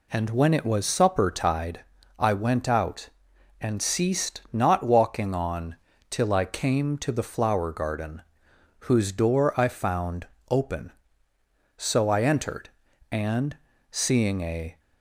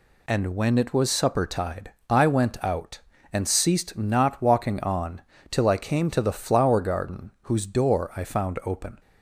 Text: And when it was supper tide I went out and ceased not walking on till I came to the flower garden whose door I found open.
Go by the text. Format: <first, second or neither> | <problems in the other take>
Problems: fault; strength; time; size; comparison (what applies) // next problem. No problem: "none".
second | pauses between "tide" and "I"; slight; at 1.8 s; 0.34 s long; slight in the second // pauses between "on" and "till"; slight; at 5.7 s; 0.34 s long; slight in the second // pauses between "garden" and "whose"; noticeable; at 8.2 s; 0.62 s long // pauses between "found" and "open"; slight; at 10.2 s; 0.24 s long // goes on to say "So I entered and seeing a"; strong; from 11.7 s on; 3.0 s long